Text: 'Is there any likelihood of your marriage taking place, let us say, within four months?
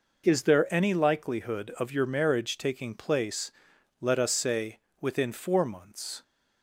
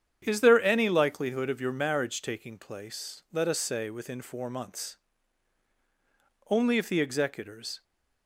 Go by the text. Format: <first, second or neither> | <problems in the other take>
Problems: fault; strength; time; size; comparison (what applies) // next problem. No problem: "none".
first | starts louder than the rest; strong; until 1.2 s; 8.5 dB // goes on to say "Only if the executors"; from 6.4 s on; 1.3 s long